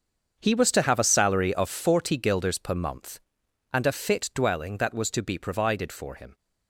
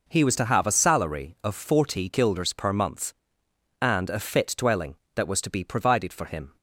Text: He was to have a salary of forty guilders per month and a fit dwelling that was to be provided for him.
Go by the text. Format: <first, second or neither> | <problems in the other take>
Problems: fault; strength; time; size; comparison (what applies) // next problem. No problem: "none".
second | gets quieter; strong; throughout; 15 dB